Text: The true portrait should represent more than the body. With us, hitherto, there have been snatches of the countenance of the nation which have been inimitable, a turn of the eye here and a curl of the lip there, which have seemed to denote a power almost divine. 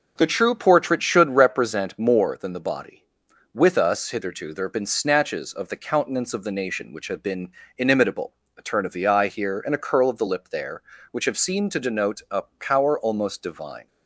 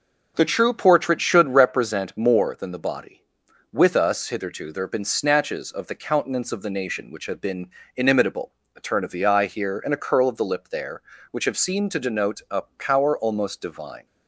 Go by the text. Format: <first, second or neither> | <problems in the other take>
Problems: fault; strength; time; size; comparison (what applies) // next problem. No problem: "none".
neither | pauses between "been" and "inimitable"; slight; the same in both // pauses between "a" and "power"; slight; the same in both